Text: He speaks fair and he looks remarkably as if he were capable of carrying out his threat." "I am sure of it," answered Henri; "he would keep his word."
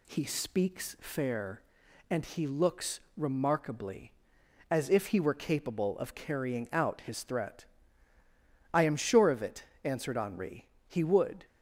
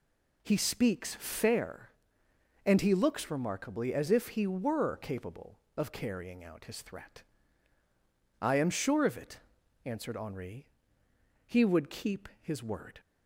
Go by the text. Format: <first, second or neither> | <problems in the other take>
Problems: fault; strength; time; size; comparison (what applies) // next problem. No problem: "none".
second | pauses between "looks" and "remarkably"; slight; at 2.9 s; 0.18 s long // stops before "keep his word"; at 11.4 s